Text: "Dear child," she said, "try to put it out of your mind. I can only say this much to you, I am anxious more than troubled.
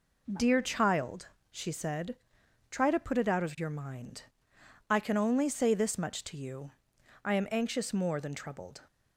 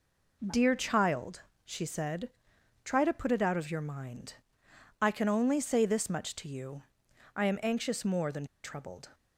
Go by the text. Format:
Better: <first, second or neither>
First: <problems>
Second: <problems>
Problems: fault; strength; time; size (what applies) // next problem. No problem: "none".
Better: first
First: none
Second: pauses between "than" and "troubled"; slight; at 8.4 s; 0.18 s long